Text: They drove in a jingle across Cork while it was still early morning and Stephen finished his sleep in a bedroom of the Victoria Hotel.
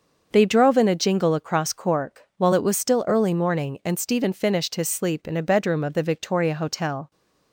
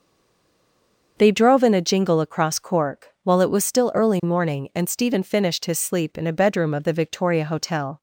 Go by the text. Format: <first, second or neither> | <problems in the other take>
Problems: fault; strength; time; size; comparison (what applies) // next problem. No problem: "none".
first | stays silent before the first word; noticeable; until 1.1 s; 1.1 s long // starts louder than the rest; until 2.1 s; 6.5 dB; also in the first // pauses between "Cork" and "while"; slight; at 3.0 s; 0.16 s long; slight in the first